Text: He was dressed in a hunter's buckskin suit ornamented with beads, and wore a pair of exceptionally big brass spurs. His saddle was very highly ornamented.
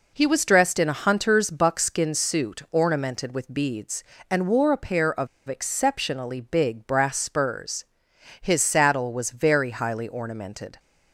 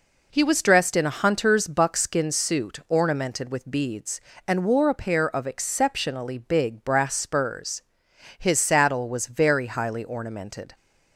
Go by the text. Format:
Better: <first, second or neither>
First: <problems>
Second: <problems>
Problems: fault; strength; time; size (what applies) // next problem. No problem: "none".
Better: second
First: pauses between "of" and "exceptionally"; slight; at 5.2 s; 0.19 s long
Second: none